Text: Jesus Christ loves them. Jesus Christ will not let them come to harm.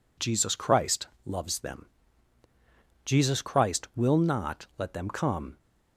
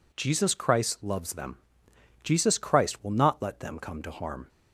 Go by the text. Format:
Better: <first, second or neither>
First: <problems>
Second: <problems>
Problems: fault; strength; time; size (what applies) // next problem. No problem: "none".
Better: second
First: pauses between "Christ" and "loves"; slight; at 1.0 s; 0.18 s long // stops before "to harm"; at 5.5 s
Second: none